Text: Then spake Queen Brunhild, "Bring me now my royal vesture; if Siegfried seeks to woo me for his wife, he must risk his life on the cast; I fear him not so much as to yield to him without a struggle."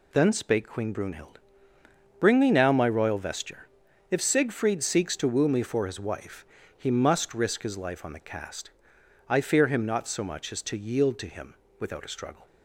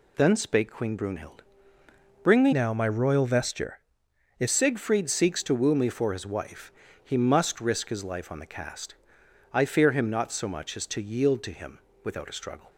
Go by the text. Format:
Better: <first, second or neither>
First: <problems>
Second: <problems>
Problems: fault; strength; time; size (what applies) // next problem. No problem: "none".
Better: first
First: pauses between "him" and "without"; slight; at 11.5 s; 0.26 s long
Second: changes voice from "now" to "if"; from 2.5 to 4.4 s; 1.9 s long // pauses between "him" and "without"; slight; at 11.7 s; 0.26 s long